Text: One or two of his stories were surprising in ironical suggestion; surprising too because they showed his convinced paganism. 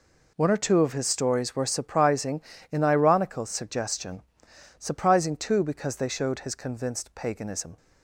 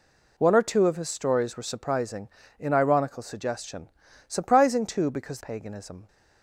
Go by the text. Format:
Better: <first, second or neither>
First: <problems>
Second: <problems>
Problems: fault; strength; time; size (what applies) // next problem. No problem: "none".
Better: first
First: none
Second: skips "they showed his convinced"; at 5.4 s